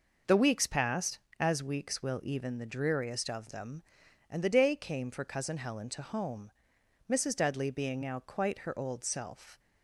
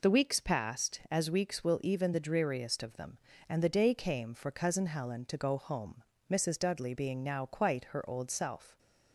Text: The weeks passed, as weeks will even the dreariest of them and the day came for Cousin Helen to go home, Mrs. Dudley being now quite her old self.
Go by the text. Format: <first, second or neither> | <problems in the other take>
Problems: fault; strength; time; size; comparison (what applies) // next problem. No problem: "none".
second | skips "go"; at 6.0 s